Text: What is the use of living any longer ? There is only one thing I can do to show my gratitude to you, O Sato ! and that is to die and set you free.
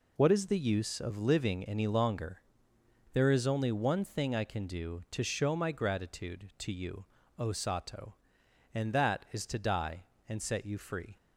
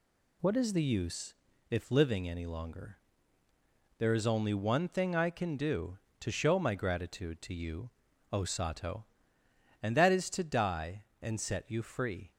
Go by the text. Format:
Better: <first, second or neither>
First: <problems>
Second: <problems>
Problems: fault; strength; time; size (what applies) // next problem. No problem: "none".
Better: first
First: none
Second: says "if" for "of"; at 1.6 s